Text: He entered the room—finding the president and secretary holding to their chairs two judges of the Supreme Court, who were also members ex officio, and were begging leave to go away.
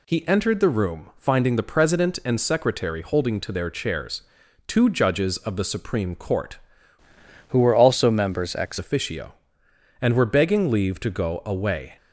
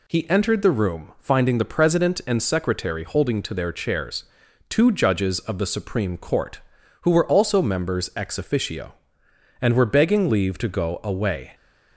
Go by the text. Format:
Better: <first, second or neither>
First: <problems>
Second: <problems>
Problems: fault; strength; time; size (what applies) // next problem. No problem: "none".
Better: second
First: pauses between "chairs" and "two"; noticeable; at 4.2 s; 0.46 s long // changes voice from "who" to "ex"; from 7.4 to 8.7 s; 1.3 s long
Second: pauses between "chairs" and "two"; noticeable; at 4.2 s; 0.46 s long